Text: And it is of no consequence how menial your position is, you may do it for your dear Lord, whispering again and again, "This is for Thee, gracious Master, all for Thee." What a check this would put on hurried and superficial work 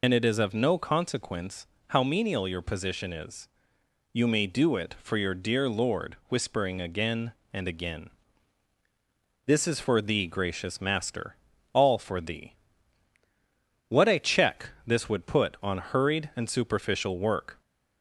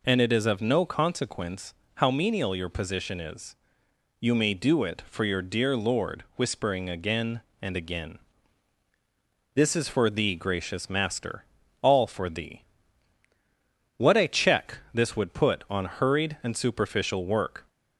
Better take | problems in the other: second | loses the start of "And"; at 0.0 s; 70 ms // pauses between "consequence" and "how"; slight; at 1.6 s; 0.22 s long; slight in the second // pauses between "check" and "this"; slight; at 14.6 s; 0.16 s long; slight in the second

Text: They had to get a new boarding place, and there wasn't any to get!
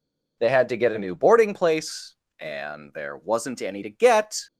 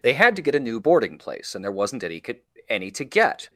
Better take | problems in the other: first | says "any" twice; at 2.6 s

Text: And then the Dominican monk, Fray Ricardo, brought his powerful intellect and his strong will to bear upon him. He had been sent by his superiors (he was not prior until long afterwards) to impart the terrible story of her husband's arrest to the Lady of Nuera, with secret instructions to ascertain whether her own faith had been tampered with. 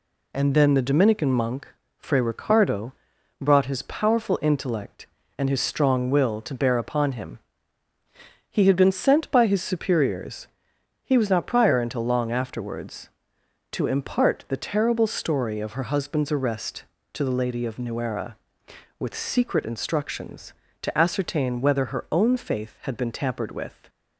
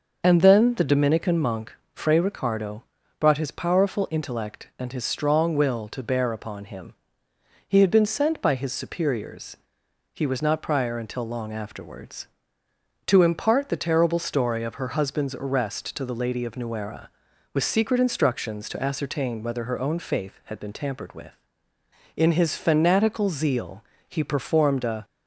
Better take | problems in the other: first | goes on to say "In his fanatical zeal he performed a"; strong; from 22.1 s on; 2.9 s long

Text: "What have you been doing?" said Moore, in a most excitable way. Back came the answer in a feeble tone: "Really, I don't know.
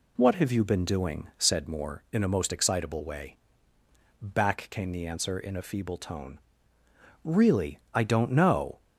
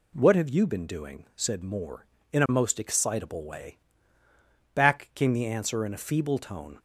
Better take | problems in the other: first | stops before "Really I don't know"; at 6.7 s

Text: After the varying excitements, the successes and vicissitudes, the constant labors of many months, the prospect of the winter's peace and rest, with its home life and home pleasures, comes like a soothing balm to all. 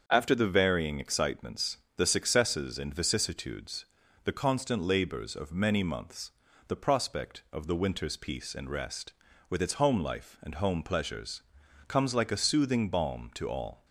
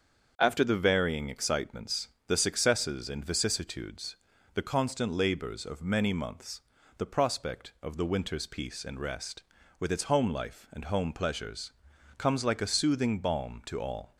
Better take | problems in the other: neither | starts louder than the rest; the same in both

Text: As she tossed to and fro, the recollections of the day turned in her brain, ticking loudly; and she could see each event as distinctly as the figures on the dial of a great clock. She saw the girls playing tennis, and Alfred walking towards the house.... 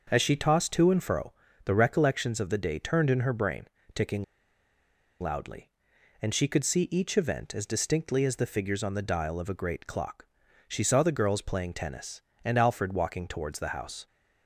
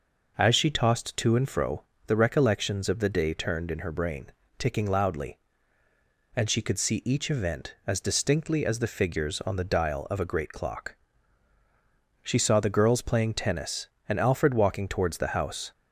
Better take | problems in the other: second | starts louder than the rest; noticeable; until 1.1 s; 6 dB // pauses between "ticking" and "loudly"; at 4.2 s; 0.98 s long

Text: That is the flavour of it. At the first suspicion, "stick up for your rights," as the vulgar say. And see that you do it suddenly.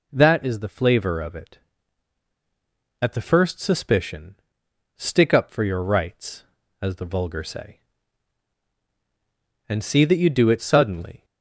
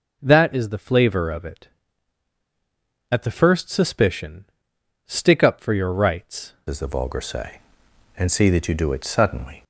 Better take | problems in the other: first | changes voice at "as"; from 6.6 s on; 3.0 s long

